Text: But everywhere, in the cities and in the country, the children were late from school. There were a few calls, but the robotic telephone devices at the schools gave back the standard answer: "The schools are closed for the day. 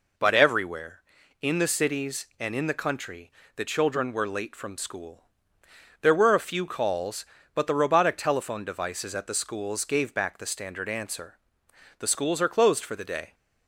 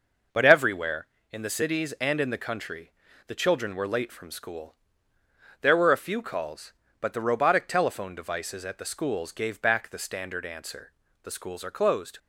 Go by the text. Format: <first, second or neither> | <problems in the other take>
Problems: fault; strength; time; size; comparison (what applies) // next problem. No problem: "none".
first | stops before "for the day"; at 12.1 s